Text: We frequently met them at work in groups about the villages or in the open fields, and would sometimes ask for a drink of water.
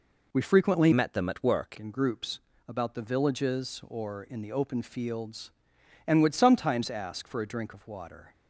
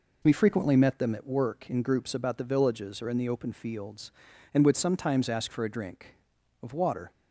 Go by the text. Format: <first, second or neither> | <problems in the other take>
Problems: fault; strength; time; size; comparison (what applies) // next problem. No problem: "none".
second | changes voice from "met" to "work"; from 0.9 to 1.7 s; 0.8 s long // pauses between "groups" and "about"; slight; at 2.4 s; 0.26 s long